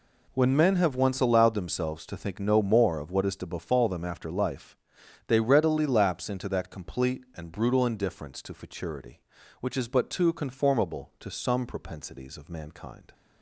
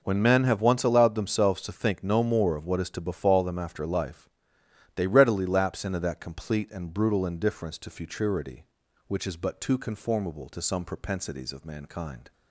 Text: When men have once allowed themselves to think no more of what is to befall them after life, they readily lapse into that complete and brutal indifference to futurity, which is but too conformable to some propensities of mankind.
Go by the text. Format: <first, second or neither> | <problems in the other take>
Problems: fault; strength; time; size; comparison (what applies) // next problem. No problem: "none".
neither | none